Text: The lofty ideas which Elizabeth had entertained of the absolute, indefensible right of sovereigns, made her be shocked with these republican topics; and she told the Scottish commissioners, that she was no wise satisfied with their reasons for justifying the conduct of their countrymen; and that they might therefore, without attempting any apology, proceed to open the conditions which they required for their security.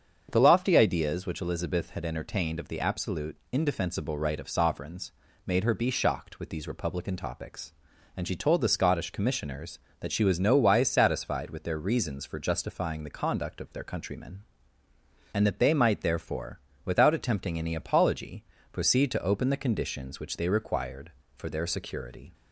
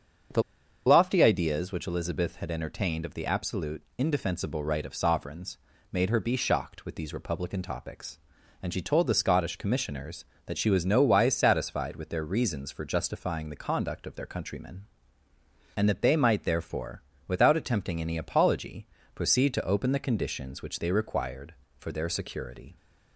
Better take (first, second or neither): first